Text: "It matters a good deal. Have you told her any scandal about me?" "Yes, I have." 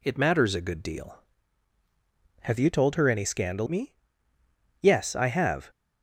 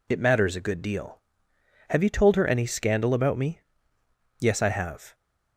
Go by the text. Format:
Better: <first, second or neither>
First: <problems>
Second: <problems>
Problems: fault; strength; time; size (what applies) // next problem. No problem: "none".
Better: second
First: skips "about"; at 3.6 s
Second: none